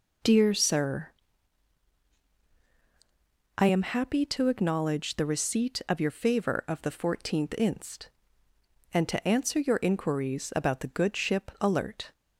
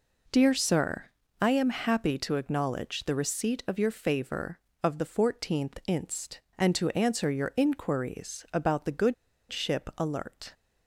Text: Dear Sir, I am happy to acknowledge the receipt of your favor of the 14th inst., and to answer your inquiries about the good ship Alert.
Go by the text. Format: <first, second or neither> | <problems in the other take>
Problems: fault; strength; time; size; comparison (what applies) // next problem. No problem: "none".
first | pauses between "good" and "ship"; at 9.1 s; 0.36 s long